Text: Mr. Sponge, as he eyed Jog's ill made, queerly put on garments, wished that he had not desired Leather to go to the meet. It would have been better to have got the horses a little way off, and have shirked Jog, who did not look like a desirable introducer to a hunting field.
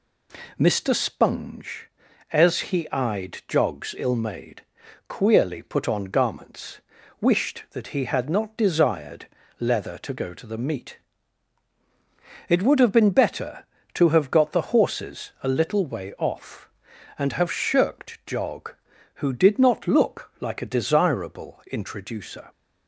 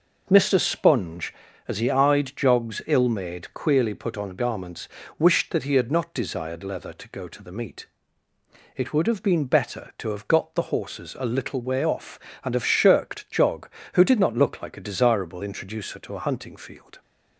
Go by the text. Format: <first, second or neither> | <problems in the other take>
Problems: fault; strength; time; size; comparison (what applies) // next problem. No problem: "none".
second | pauses between "desired" and "Leather"; slight; at 9.2 s; 0.34 s long // stops before "to a hunting field"; at 22.5 s